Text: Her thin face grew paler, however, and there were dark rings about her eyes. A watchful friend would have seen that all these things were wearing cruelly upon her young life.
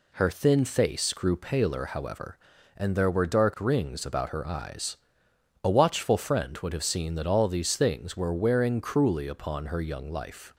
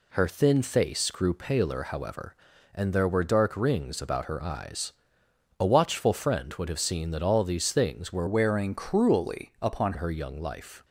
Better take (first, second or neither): first